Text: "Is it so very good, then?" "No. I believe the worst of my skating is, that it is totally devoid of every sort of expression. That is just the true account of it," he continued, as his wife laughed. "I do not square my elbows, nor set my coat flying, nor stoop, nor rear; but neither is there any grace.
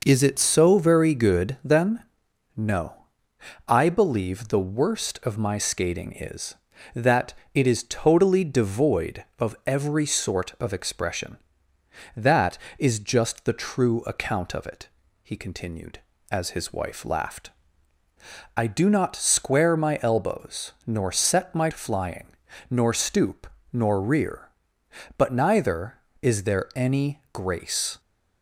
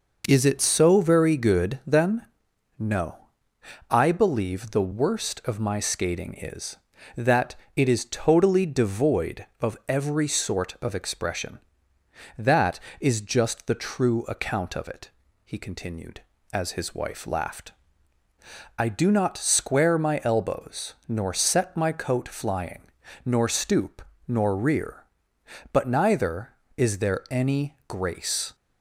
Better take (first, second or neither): second